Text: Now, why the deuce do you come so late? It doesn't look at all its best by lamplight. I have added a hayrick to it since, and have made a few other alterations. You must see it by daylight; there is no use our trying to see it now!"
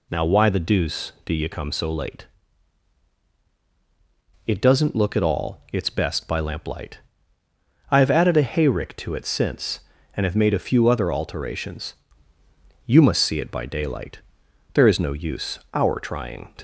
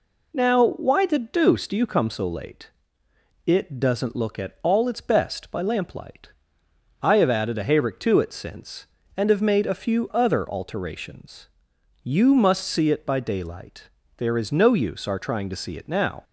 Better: second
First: pauses between "use" and "our"; slight; at 15.5 s; 0.16 s long // stops before "see it now"; at 16.5 s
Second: none

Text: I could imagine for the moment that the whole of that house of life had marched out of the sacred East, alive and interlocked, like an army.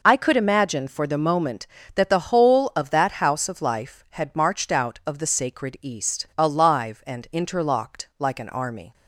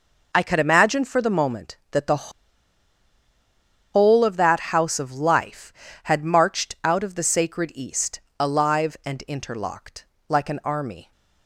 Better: first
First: none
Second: pauses between "the" and "whole"; strong; at 2.2 s; 1.6 s long

